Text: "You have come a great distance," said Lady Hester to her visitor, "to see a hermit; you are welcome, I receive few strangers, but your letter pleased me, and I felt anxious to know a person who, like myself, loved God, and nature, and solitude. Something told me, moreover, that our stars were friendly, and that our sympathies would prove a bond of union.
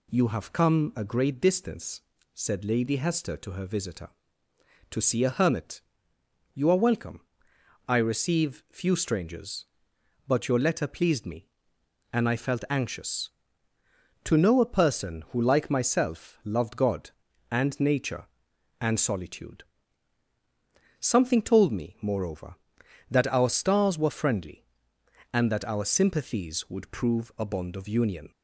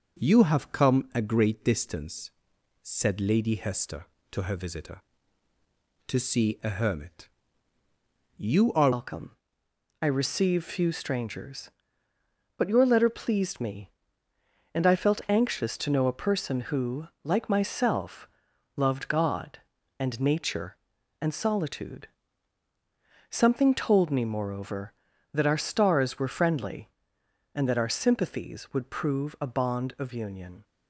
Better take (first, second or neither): first